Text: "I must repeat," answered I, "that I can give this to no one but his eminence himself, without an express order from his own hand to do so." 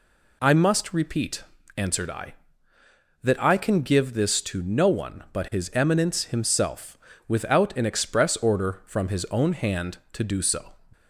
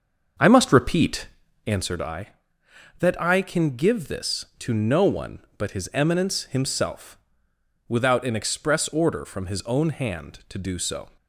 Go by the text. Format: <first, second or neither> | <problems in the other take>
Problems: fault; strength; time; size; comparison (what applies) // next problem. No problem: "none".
first | starts louder than the rest; until 1.9 s; 6.5 dB